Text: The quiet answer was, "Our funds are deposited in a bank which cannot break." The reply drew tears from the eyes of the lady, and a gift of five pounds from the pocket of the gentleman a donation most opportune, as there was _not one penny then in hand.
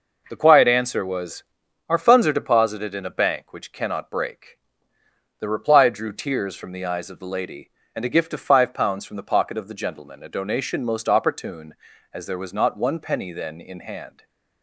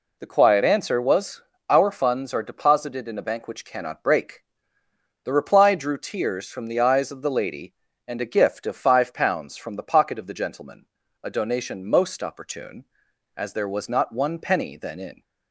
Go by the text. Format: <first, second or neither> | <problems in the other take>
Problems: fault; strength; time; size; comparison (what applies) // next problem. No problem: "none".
first | pauses between "gentleman" and "a"; slight; at 10.8 s; 0.36 s long // stops before "hand"; at 15.2 s